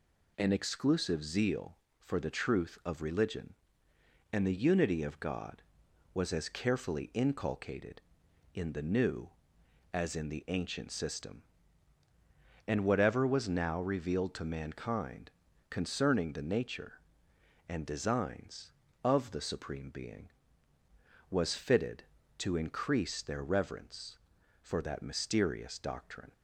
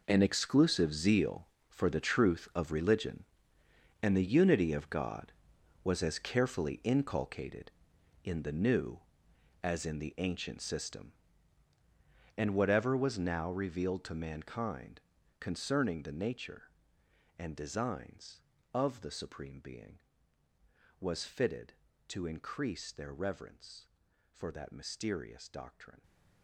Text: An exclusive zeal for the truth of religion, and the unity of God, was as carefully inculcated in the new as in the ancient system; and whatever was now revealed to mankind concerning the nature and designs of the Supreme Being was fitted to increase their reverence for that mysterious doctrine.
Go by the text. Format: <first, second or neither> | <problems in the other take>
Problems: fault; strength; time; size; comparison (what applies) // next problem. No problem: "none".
first | gets quieter; strong; throughout; 14 dB // pauses between "mankind" and "concerning"; at 15.0 s; 0.40 s long; also in the first